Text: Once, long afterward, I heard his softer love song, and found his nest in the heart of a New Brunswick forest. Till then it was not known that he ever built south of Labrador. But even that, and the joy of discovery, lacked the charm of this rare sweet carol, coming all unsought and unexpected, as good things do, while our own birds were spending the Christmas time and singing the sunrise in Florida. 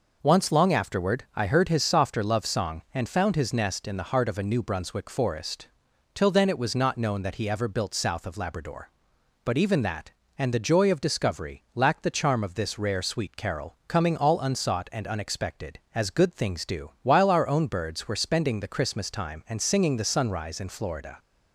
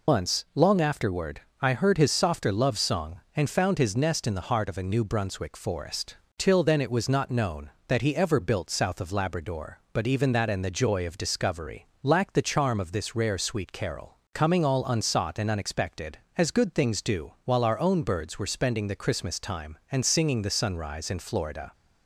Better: first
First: none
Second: loses the start of "Once"; at 0.0 s; 85 ms

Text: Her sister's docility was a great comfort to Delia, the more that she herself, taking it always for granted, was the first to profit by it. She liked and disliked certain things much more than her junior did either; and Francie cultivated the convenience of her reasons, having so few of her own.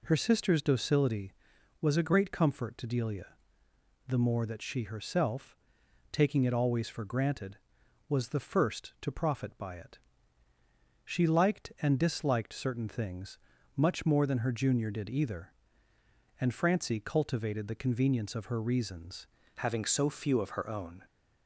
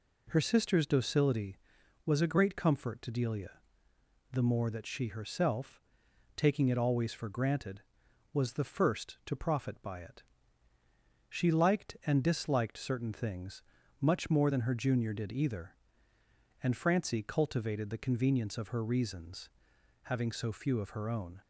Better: second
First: pauses between "things" and "much"; at 13.3 s; 0.40 s long // changes voice at "having"; from 19.5 s on; 1.5 s long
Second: pauses between "things" and "much"; at 13.6 s; 0.40 s long

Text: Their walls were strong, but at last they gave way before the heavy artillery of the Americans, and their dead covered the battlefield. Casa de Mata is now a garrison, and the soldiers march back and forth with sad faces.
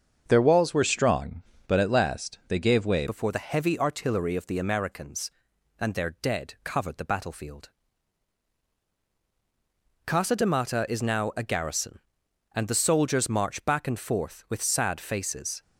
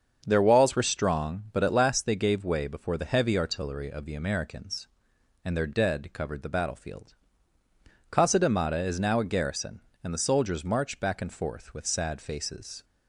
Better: second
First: starts louder than the rest; until 1.2 s; 6.5 dB // changes voice at "before"; from 3.0 s on; 12.6 s long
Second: starts louder than the rest; until 1.2 s; 7 dB

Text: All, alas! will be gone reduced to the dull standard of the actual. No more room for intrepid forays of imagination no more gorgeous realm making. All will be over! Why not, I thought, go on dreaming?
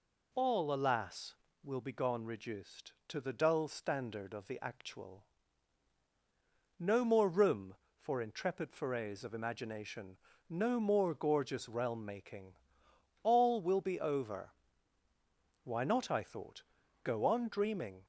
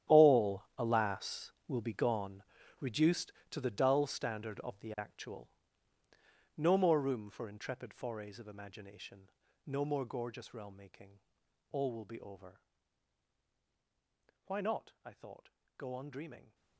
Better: first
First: pauses between "imagination" and "no"; slight; at 10.1 s; 0.32 s long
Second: gets quieter; strong; throughout; 15.5 dB // pauses between "gone" and "reduced"; at 2.4 s; 0.38 s long // pauses between "imagination" and "no"; slight; at 9.2 s; 0.36 s long

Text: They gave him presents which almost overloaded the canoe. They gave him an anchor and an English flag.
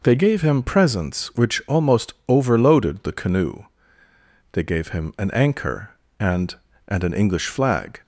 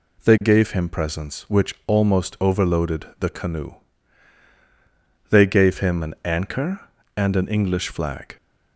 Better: second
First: says "and" twice; at 6.8 s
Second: none

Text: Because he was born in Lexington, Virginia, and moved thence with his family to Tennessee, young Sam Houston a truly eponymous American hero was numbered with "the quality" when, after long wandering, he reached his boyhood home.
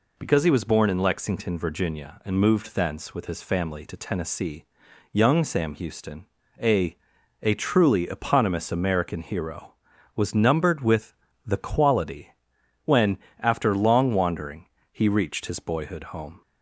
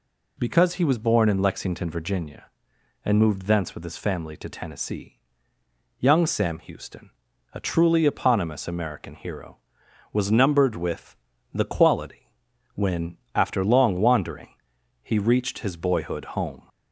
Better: second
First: pauses between "Houston" and "a"; slight; at 6.2 s; 0.36 s long // says "a" twice; at 7.4 s // pauses between "with" and "the"; slight; at 11.1 s; 0.32 s long // pauses between "quality" and "when"; noticeable; at 12.3 s; 0.54 s long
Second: pauses between "Houston" and "a"; at 7.1 s; 0.44 s long // pauses between "with" and "the"; slight; at 11.1 s; 0.36 s long // pauses between "quality" and "when"; at 12.3 s; 0.44 s long

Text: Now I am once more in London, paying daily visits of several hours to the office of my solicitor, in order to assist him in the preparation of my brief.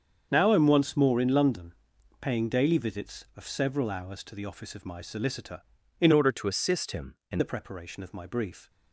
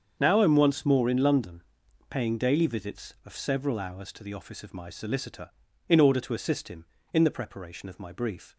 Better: second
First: starts louder than the rest; strong; until 1.3 s; 7.5 dB // changes voice from "order" to "in"; from 6.1 to 7.3 s; 1.2 s long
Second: starts louder than the rest; until 1.2 s; 7 dB

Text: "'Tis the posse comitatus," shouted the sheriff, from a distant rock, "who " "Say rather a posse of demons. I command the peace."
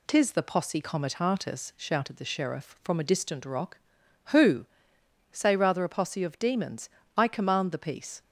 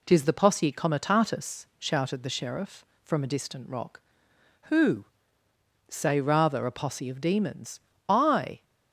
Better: first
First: none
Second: stops before "command the peace"; at 8.6 s

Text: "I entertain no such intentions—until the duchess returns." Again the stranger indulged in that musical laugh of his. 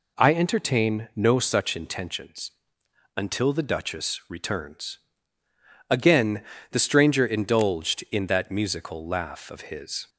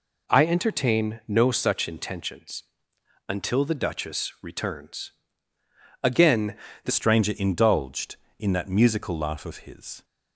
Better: first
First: pauses between "Again" and "the"; slight; at 6.4 s; 0.28 s long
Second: pauses between "Again" and "the"; slight; at 6.5 s; 0.28 s long // changes voice at "stranger"; from 6.8 s on; 3.2 s long

